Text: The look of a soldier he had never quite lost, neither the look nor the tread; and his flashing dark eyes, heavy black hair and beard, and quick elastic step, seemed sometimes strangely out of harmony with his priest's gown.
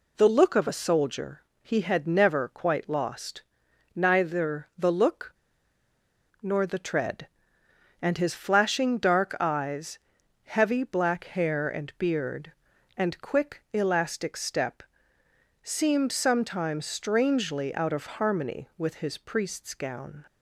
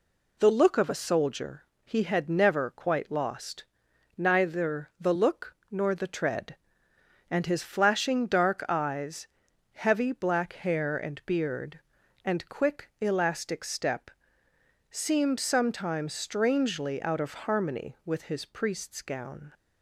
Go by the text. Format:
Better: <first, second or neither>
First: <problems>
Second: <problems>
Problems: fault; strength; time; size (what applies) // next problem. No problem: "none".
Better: second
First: pauses between "soldier" and "he"; slight; at 1.4 s; 0.20 s long // pauses between "look" and "nor"; at 5.3 s; 1.0 s long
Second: pauses between "soldier" and "he"; slight; at 1.6 s; 0.20 s long